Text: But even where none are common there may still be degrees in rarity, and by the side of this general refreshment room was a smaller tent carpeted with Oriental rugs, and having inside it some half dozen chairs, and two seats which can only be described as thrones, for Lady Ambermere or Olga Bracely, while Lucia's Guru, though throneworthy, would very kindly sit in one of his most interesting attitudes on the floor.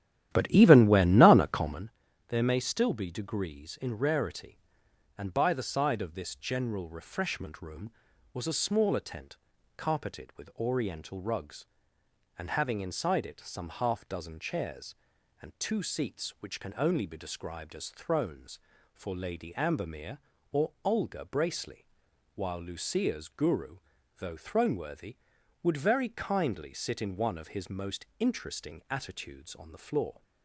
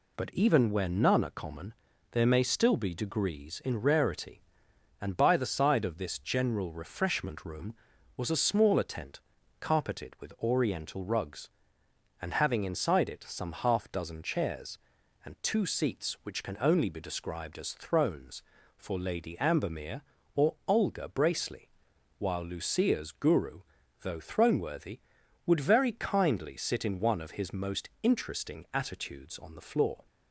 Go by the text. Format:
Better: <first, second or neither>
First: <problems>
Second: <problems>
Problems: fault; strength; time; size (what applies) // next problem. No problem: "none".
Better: second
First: starts louder than the rest; strong; until 1.9 s; 12 dB // pauses between "common" and "there"; at 1.9 s; 0.38 s long // pauses between "tent" and "carpeted"; at 9.3 s; 0.40 s long // pauses between "or" and "Olga"; slight; at 20.7 s; 0.16 s long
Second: pauses between "common" and "there"; at 1.7 s; 0.38 s long // pauses between "tent" and "carpeted"; at 9.1 s; 0.40 s long // pauses between "or" and "Olga"; slight; at 20.5 s; 0.16 s long